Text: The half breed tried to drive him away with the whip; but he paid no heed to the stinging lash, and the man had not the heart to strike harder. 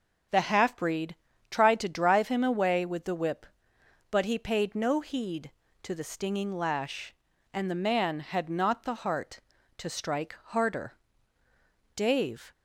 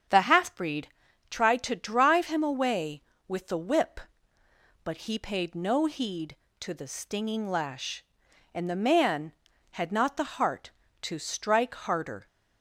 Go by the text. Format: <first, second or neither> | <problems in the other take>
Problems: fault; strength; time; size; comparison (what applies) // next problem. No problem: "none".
second | starts louder than the rest; strong; until 1.6 s; 7 dB; strong in the second // pauses between "breed" and "tried"; slight; at 1.1 s; 0.34 s long; also in the second // goes on to say "Dave"; from 11.9 s on; 0.56 s long